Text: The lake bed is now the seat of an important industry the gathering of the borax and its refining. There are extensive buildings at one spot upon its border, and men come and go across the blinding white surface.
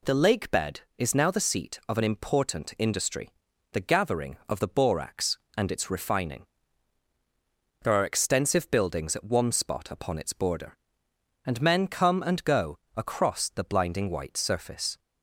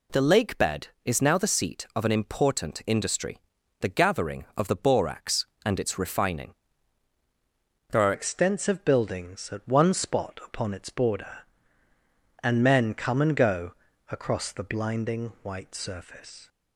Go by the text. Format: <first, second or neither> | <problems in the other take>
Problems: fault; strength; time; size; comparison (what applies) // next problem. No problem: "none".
first | pauses between "industry" and "the"; at 3.3 s; 0.40 s long; also in the first // changes voice at "extensive"; from 8.1 s on; 8.3 s long // pauses between "go" and "across"; at 13.7 s; 0.38 s long; slight in the first